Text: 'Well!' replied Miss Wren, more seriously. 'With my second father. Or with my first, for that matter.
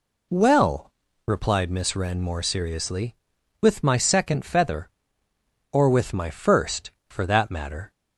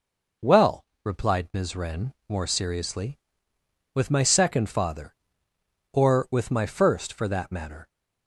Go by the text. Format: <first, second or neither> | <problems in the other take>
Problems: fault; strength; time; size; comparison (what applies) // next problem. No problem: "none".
second | says "feather" for "father"; at 4.4 s